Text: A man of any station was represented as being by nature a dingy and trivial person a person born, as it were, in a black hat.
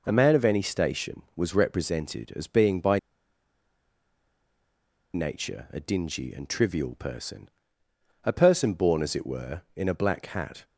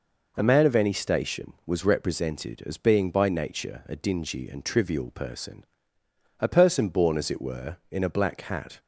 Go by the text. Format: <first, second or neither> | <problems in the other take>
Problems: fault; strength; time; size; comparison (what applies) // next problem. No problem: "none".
second | pauses between "by" and "nature"; strong; at 2.9 s; 2.1 s long // pauses between "person" and "a"; noticeable; at 7.4 s; 0.78 s long; noticeable in the second